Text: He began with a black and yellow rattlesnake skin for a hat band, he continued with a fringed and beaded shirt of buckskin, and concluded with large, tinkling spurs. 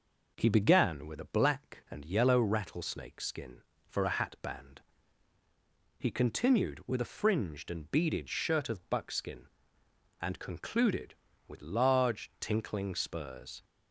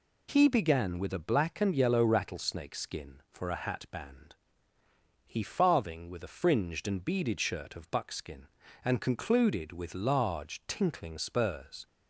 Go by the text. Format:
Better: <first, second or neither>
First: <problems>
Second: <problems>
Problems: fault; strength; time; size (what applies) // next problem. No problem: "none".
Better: first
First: none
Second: says "farthing" for "continued"; at 5.4 s